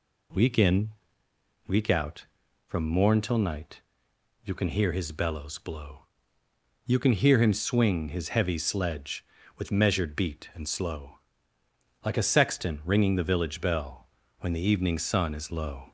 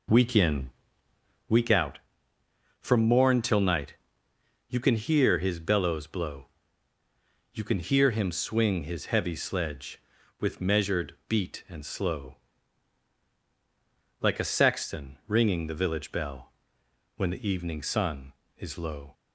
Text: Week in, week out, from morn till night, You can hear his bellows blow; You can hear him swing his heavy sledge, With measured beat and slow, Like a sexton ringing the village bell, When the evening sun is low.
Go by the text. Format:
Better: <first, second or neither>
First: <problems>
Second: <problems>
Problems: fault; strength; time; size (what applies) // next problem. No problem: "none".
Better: first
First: none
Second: starts louder than the rest; noticeable; until 1.6 s; 4.5 dB